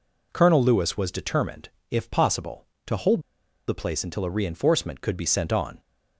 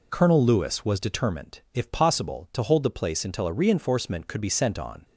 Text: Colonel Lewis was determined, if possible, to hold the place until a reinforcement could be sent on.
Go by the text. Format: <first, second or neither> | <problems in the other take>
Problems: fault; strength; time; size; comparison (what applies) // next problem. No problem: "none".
second | pauses between "hold" and "the"; noticeable; at 3.2 s; 0.46 s long